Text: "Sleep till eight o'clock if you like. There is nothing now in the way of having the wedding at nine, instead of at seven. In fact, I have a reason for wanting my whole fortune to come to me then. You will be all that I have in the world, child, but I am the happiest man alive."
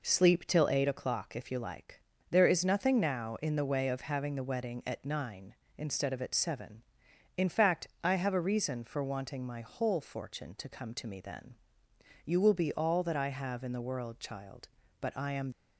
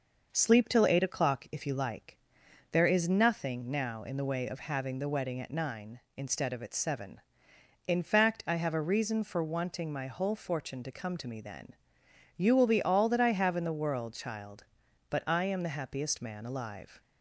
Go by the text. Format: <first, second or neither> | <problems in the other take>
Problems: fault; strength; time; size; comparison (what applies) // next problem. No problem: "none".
second | stops before "the happiest man alive"; at 15.5 s